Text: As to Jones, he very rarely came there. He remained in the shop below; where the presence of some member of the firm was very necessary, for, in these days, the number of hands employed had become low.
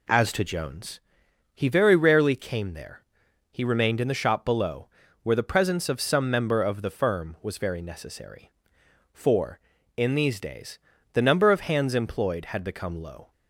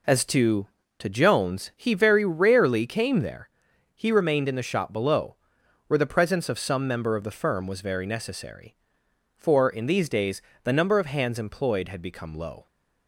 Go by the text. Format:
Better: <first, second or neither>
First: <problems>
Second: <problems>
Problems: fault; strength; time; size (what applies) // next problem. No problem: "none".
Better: first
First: none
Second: says "to" twice; at 0.9 s